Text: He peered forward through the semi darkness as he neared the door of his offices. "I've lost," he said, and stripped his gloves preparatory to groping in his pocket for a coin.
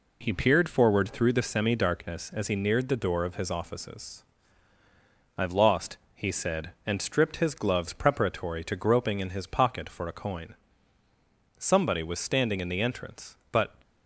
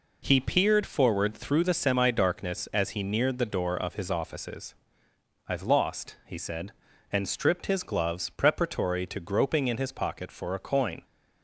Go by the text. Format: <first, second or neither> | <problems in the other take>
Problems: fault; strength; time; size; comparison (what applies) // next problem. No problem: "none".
second | goes on to say "Somebody was standing in the entrance but"; strong; from 11.5 s on; 2.1 s long